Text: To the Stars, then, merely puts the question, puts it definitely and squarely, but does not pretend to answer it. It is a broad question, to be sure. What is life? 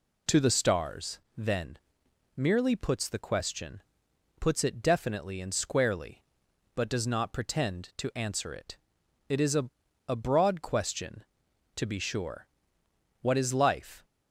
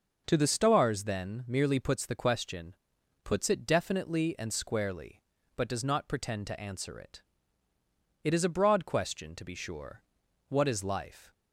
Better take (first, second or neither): second